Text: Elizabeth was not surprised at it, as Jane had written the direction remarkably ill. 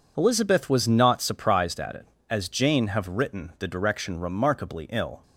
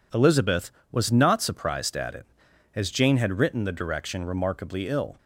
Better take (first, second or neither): second